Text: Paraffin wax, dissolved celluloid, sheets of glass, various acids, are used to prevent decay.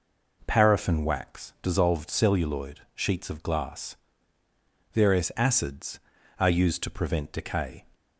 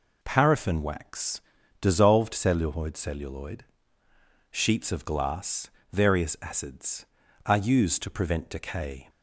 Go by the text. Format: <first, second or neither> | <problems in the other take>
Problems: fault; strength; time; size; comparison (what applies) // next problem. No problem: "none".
first | says "celluloid" twice; at 2.9 s